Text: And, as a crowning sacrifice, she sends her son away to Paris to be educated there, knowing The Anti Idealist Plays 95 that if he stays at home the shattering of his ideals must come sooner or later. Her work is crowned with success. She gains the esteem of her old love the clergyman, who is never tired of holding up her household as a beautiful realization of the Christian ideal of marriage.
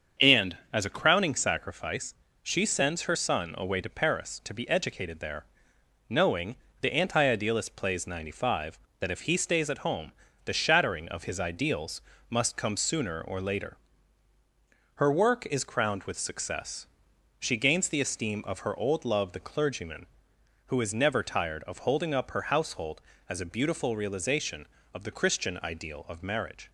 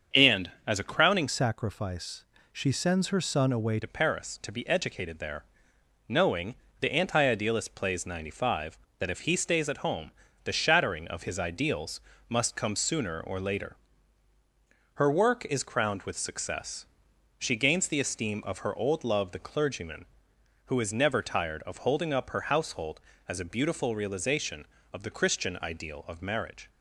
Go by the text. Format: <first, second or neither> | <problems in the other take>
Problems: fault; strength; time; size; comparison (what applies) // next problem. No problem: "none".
first | starts louder than the rest; strong; until 1.3 s; 7.5 dB; strong in the first // changes voice from "sacrifice" to "away"; from 1.2 to 3.8 s; 2.6 s long // pauses between "knowing" and "The"; slight; at 6.5 s; 0.24 s long; slight in the first // pauses between "home" and "the"; slight; at 10.1 s; 0.34 s long; slight in the first // pauses between "ideals" and "must"; slight; at 11.9 s; 0.30 s long; slight in the first